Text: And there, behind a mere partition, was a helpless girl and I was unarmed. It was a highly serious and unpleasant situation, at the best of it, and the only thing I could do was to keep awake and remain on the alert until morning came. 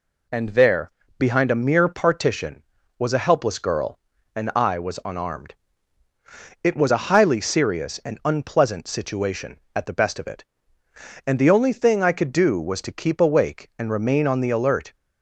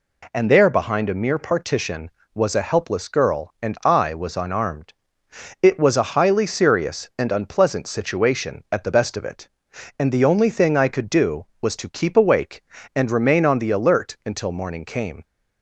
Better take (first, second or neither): second